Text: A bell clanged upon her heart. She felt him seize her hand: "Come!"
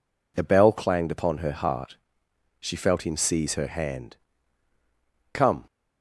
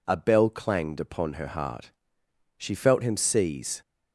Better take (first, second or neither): first